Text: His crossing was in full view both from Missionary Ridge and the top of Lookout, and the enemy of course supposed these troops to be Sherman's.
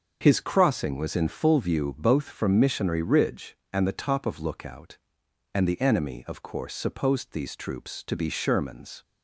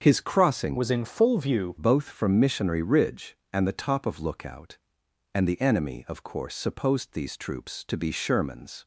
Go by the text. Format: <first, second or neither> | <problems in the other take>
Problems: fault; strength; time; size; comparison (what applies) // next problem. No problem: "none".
first | starts louder than the rest; until 1.0 s; 7 dB; also in the first // changes voice from "was" to "view"; from 0.7 to 1.7 s; 1.0 s long